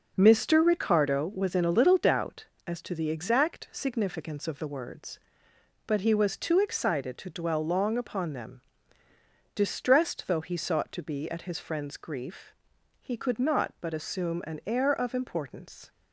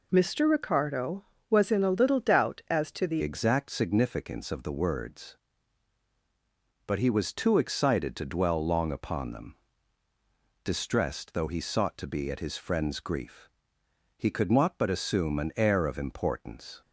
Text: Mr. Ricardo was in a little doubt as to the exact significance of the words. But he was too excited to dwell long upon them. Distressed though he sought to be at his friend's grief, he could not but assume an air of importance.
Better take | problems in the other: first | changes voice at "exact"; from 3.2 s on; 13.6 s long

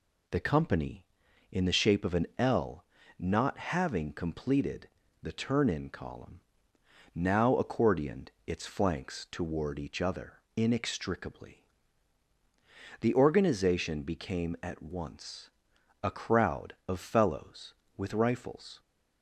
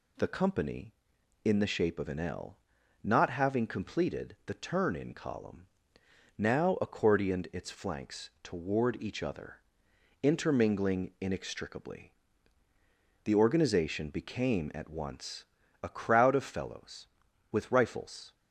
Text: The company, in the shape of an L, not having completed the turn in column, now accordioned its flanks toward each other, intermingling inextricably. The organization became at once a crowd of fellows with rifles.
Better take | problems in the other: second | pauses between "completed" and "the"; slight; at 4.8 s; 0.32 s long // pauses between "accordioned" and "its"; slight; at 8.2 s; 0.18 s long // skips "intermingling"; at 10.4 s // pauses between "once" and "a"; noticeable; at 15.4 s; 0.54 s long; slight in the second

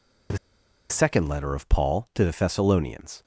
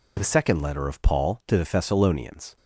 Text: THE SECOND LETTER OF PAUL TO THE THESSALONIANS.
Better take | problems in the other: second | pauses between "THE" and "SECOND"; noticeable; at 0.3 s; 0.52 s long

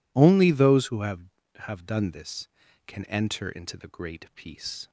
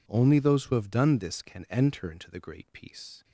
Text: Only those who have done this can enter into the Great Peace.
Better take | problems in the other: second | says "have" twice; at 1.5 s

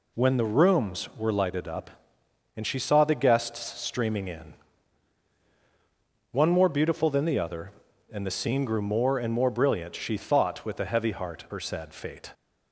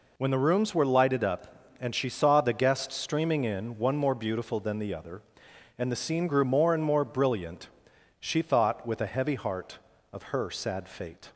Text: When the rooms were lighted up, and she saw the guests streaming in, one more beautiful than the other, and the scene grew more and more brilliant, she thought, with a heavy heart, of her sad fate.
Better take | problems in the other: second | skips "of"; at 11.4 s

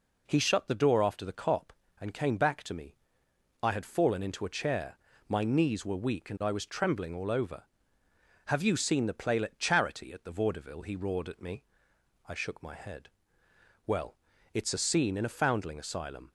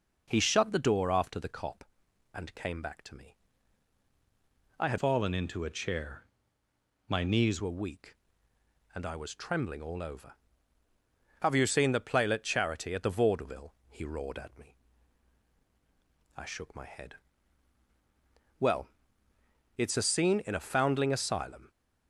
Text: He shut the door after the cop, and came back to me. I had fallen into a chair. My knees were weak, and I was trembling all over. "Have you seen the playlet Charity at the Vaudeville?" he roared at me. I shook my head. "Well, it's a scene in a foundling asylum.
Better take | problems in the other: first | changes voice from "fallen" to "knees"; from 4.9 to 7.6 s; 2.7 s long

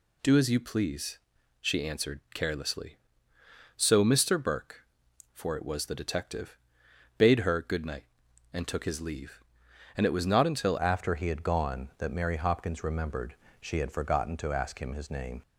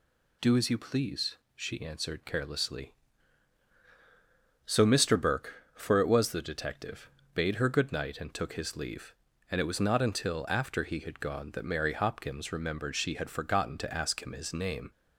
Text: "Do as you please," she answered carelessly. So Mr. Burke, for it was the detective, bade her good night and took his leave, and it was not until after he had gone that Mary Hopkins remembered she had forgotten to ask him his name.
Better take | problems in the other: second | changes voice at "after"; from 10.7 s on; 4.7 s long // pauses between "remembered" and "she"; slight; at 13.3 s; 0.26 s long

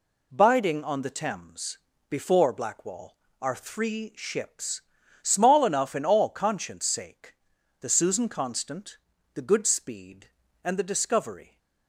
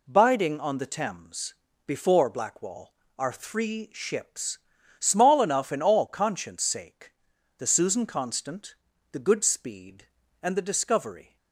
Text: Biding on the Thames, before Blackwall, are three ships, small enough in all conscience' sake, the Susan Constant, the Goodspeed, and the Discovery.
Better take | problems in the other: neither | none

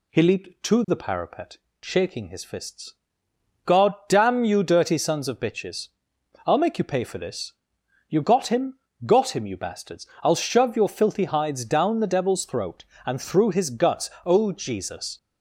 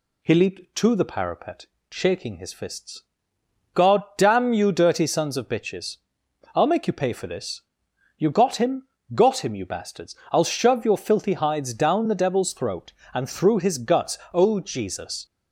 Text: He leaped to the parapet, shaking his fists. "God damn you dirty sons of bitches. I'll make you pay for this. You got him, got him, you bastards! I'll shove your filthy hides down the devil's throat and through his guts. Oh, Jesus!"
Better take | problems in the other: neither | none

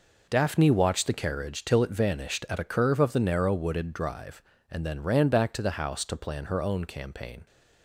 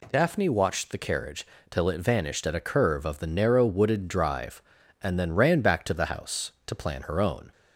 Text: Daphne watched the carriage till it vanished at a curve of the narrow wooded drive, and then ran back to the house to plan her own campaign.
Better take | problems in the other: first | pauses between "carriage" and "till"; slight; at 1.4 s; 0.24 s long // stops before "campaign"; at 7.5 s

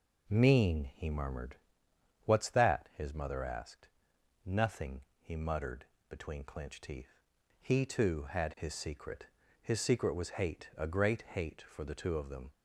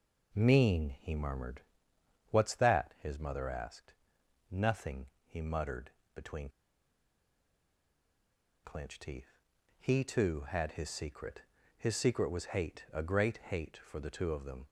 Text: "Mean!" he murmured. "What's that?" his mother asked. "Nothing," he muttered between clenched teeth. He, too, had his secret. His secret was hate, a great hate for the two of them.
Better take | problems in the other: first | pauses between "muttered" and "between"; slight; at 5.9 s; 0.24 s long; slight in the first // pauses between "between" and "clenched"; strong; at 6.4 s; 2.1 s long

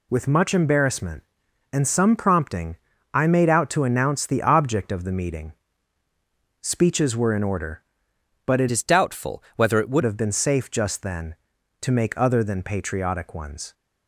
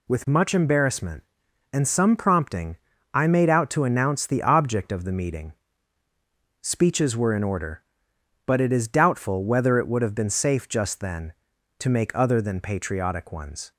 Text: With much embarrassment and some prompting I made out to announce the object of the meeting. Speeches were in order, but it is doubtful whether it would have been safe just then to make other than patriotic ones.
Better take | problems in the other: second | pauses between "prompting" and "I"; slight; at 2.7 s; 0.36 s long; slight in the second // changes voice from "is" to "would"; from 8.7 to 10.0 s; 1.3 s long

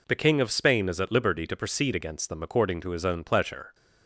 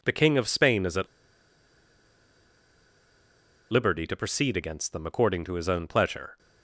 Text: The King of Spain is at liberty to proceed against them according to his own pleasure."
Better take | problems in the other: first | pauses between "at" and "liberty"; strong; at 1.0 s; 2.6 s long

